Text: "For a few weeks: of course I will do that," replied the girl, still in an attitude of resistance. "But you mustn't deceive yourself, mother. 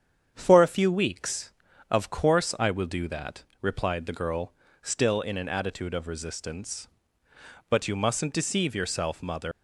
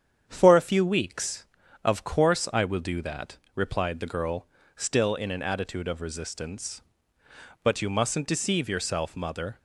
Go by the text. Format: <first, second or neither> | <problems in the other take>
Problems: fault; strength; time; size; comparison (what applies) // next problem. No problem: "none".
second | starts louder than the rest; strong; until 1.3 s; 8 dB; strong in the second // leaves "mother" unfinished; at 9.5 s; 125 ms